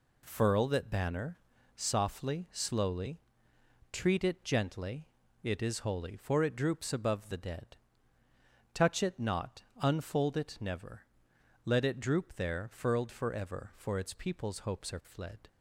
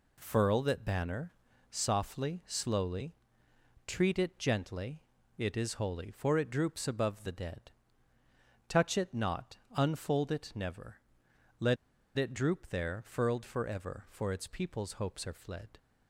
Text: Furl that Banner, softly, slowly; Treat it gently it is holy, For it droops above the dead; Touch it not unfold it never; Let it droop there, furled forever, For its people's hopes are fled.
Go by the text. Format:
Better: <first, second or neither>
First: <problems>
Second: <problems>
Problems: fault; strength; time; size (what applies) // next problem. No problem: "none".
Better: first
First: pauses between "gently" and "it"; slight; at 5.0 s; 0.36 s long // pauses between "not" and "unfold"; slight; at 9.6 s; 0.18 s long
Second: pauses between "gently" and "it"; slight; at 5.0 s; 0.36 s long // pauses between "not" and "unfold"; slight; at 9.5 s; 0.18 s long // pauses between "Let" and "it"; at 11.7 s; 0.41 s long